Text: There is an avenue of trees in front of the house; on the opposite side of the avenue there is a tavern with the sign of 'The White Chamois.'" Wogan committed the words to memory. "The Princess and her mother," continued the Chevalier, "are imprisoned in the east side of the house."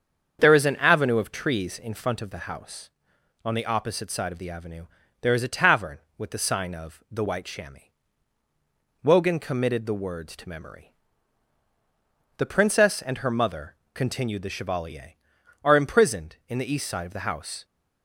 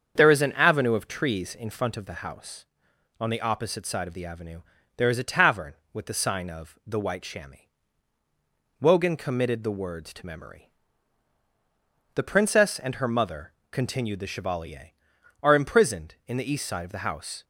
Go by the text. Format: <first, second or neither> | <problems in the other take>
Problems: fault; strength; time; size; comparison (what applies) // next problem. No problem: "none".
neither | starts louder than the rest; strong; the same in both // pauses between "avenue" and "there"; slight; the same in both